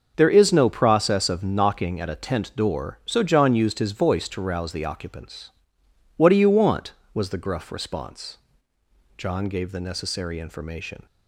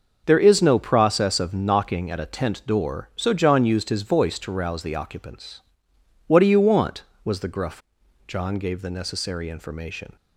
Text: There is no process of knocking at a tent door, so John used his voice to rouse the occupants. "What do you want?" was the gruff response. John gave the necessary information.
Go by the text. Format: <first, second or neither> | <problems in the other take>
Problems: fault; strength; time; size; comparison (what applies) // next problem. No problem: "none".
first | starts louder than the rest; until 1.2 s; 6 dB; also in the first // skips "response"; at 8.0 s